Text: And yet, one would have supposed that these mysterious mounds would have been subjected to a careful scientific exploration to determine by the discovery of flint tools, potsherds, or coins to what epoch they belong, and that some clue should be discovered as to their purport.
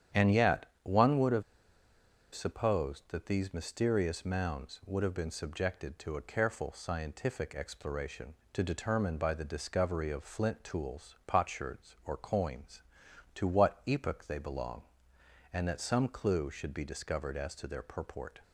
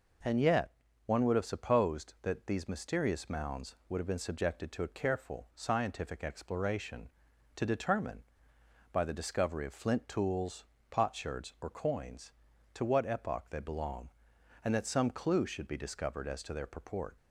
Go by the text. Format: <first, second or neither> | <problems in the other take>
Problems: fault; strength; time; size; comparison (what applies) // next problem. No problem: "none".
second | starts louder than the rest; strong; until 1.3 s; 9.5 dB // pauses between "have" and "supposed"; noticeable; at 1.4 s; 0.90 s long